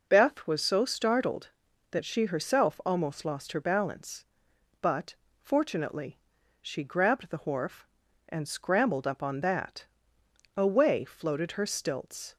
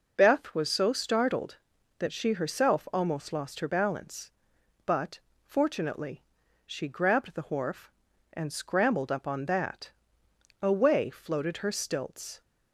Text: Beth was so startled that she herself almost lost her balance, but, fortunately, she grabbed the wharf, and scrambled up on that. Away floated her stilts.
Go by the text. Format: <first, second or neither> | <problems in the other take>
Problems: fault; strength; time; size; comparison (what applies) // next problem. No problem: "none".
neither | none